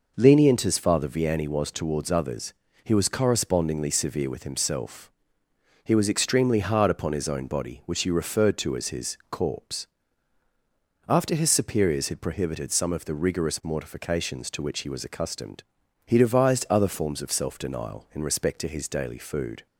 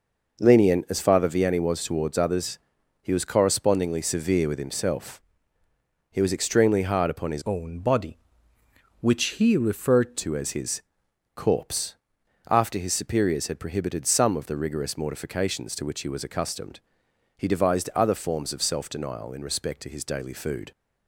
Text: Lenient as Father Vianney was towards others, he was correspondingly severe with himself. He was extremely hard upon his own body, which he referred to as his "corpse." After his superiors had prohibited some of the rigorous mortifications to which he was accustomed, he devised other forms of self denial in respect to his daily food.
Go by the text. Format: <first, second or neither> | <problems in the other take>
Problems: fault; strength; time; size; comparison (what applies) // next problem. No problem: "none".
first | changes voice from "own" to "referred"; from 7.4 to 10.1 s; 2.7 s long // pauses between "his" and "corpse"; noticeable; at 10.8 s; 0.54 s long